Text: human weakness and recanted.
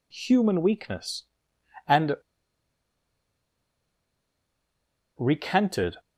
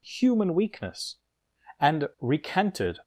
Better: second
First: pauses between "and" and "recanted"; strong; at 2.1 s; 3.0 s long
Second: none

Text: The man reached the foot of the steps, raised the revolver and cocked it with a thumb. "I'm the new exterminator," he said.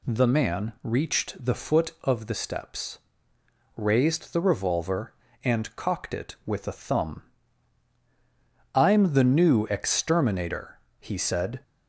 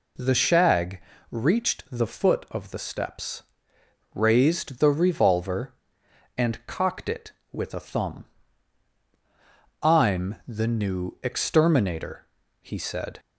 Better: first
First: none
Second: says "shag" for "man"; at 0.3 s

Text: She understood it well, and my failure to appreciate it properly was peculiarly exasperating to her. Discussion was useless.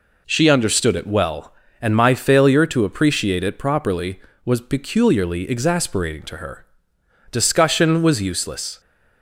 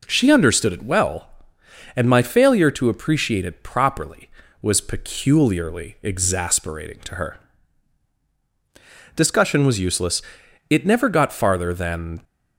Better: first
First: none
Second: goes on to say "It never got farther than"; from 10.6 s on; 1.5 s long

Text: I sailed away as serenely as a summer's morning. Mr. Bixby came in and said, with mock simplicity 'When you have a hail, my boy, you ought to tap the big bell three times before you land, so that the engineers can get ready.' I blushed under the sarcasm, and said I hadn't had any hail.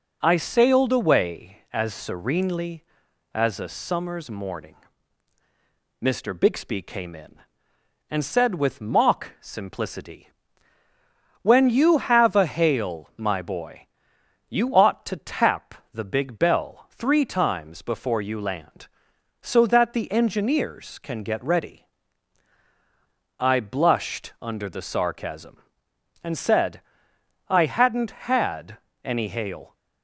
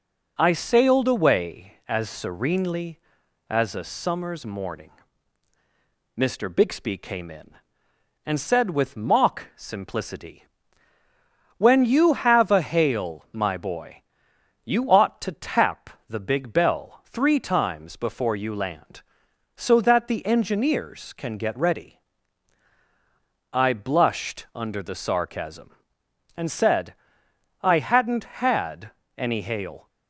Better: neither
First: pauses between "simplicity" and "When"; at 10.3 s; 1.1 s long // pauses between "tap" and "the"; slight; at 15.7 s; 0.18 s long // pauses between "said" and "I"; noticeable; at 26.8 s; 0.66 s long // pauses between "had" and "any"; slight; at 28.7 s; 0.26 s long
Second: pauses between "simplicity" and "When"; at 10.4 s; 1.1 s long // pauses between "tap" and "the"; slight; at 15.8 s; 0.18 s long // pauses between "said" and "I"; noticeable; at 26.9 s; 0.66 s long // pauses between "had" and "any"; slight; at 28.9 s; 0.26 s long

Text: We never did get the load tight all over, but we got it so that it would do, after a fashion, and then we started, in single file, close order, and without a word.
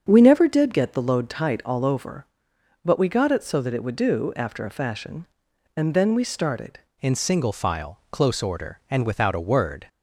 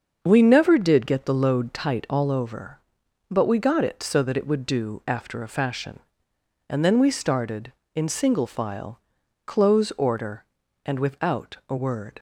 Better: second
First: starts louder than the rest; until 1.0 s; 7 dB // changes voice at "in"; from 7.0 s on; 2.8 s long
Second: starts louder than the rest; until 1.2 s; 6.5 dB

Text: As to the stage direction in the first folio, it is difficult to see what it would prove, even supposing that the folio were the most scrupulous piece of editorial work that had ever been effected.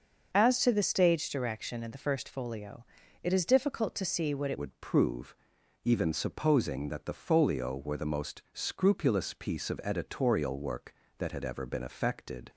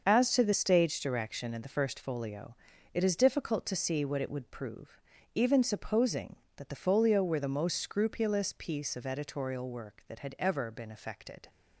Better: second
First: starts louder than the rest; until 1.3 s; 6 dB // changes voice at "would"; from 4.5 s on; 7.9 s long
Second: starts louder than the rest; until 1.0 s; 6.5 dB

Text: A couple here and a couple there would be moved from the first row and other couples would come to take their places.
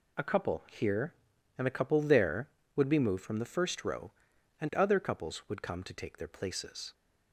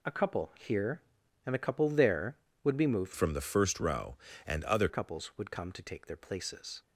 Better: first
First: none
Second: changes voice from "from" to "other"; from 3.1 to 4.8 s; 1.7 s long

